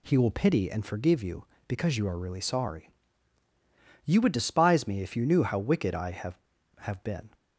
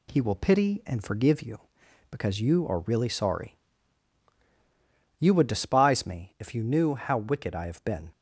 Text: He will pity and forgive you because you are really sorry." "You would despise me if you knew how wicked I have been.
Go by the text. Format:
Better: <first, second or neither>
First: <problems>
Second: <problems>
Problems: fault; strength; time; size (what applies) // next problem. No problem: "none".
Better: second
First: says "have" twice; at 6.7 s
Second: none